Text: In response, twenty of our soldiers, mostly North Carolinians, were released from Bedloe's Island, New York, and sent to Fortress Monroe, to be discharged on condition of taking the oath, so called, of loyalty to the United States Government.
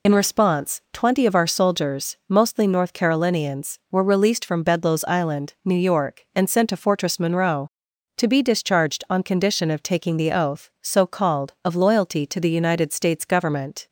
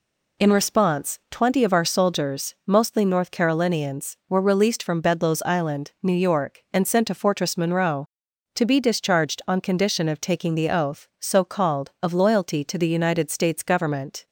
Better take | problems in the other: second | loses the start of "In"; at 0.0 s; 30 ms

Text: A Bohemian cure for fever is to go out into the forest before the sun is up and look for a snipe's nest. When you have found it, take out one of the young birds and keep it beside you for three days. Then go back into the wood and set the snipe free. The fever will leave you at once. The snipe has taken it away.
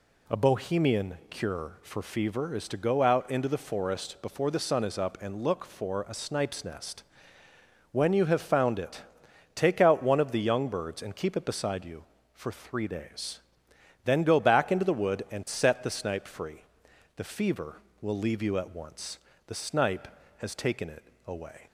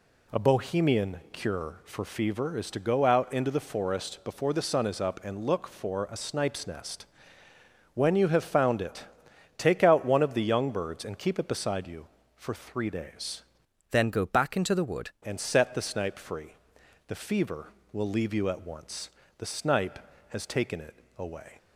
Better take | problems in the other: first | changes voice from "Then" to "wood"; from 13.9 to 15.1 s; 1.2 s long // pauses between "it" and "away"; slight; at 20.9 s; 0.24 s long; slight in the first

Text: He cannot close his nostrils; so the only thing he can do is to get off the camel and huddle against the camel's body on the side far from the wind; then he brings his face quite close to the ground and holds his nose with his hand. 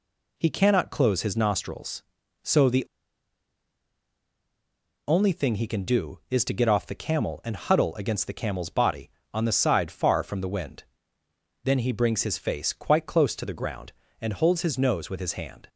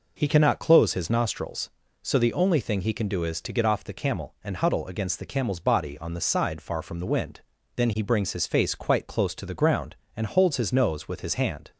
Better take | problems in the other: second | pauses between "the" and "only"; strong; at 2.8 s; 2.2 s long

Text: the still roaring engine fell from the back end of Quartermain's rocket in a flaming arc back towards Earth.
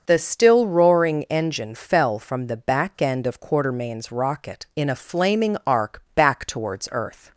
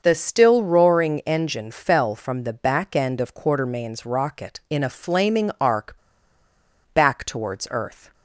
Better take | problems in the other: first | starts louder than the rest; until 1.0 s; 6.5 dB; also in the first // pauses between "arc" and "back"; noticeable; at 5.9 s; 0.97 s long

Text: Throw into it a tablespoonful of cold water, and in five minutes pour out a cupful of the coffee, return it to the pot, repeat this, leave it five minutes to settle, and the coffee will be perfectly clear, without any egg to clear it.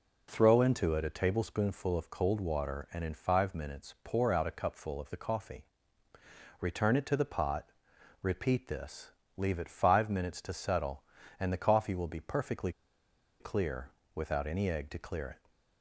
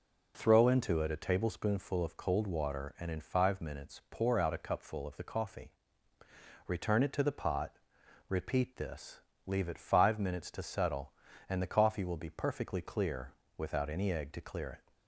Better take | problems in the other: second | pauses between "perfectly" and "clear"; noticeable; at 12.7 s; 0.68 s long

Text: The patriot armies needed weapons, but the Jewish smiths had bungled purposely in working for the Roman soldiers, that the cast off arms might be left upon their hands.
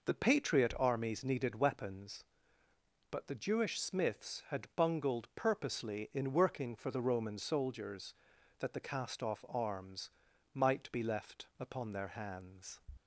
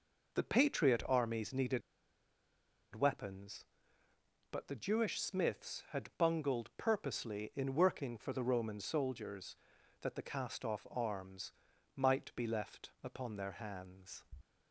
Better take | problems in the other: first | pauses between "needed" and "weapons"; at 1.8 s; 1.1 s long // pauses between "arms" and "might"; noticeable; at 11.5 s; 0.46 s long; noticeable in the first

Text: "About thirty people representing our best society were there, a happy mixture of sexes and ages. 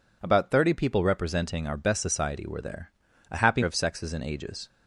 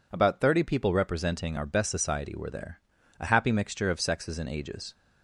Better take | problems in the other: second | skips "mixture"; at 3.6 s

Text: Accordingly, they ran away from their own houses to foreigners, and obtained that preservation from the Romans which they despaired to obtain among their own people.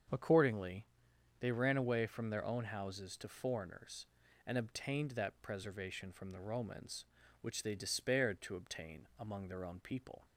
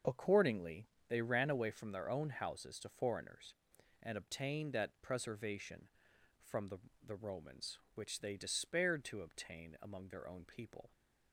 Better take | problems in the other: first | starts louder than the rest; until 1.2 s; 6.5 dB; strong in the first // says "the" twice; at 7.0 s

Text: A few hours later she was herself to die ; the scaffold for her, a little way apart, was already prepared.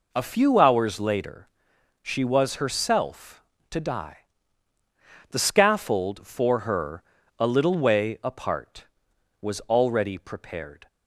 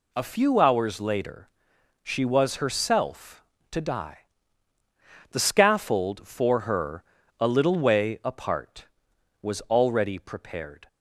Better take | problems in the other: second | starts louder than the rest; noticeable; until 1.2 s; 4 dB // pauses between "later" and "she"; noticeable; at 1.4 s; 0.56 s long; noticeable in the second

